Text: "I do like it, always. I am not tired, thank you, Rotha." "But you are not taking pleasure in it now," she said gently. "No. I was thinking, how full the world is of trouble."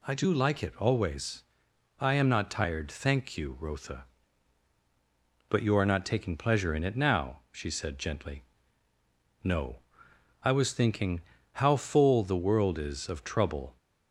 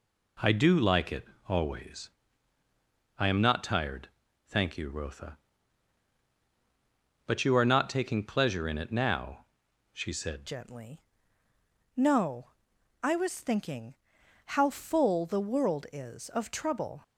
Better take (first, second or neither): first